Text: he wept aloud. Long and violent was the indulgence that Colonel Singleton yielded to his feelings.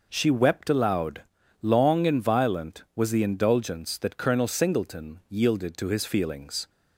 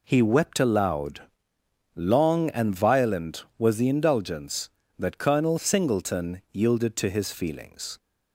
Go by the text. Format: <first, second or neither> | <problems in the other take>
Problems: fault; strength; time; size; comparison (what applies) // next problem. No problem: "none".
second | says "she" for "he"; at 0.0 s